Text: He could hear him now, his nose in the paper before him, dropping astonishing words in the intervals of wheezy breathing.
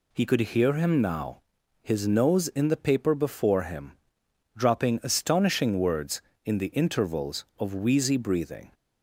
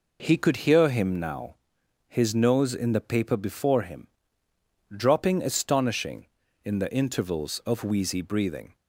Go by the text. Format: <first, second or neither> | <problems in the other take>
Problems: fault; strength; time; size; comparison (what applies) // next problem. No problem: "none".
first | skips "words"; at 6.4 s